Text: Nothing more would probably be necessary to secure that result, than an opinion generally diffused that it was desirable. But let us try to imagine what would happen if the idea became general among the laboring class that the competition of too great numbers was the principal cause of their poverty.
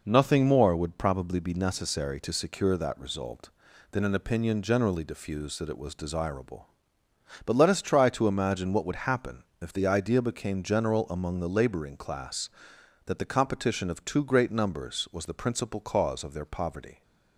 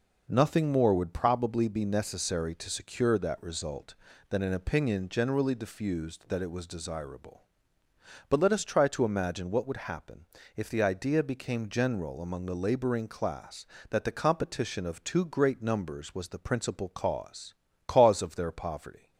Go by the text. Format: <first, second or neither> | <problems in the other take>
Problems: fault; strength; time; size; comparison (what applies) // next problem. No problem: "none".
first | pauses between "happen" and "if"; slight; at 10.2 s; 0.30 s long; slight in the first // says "cause" twice; at 17.8 s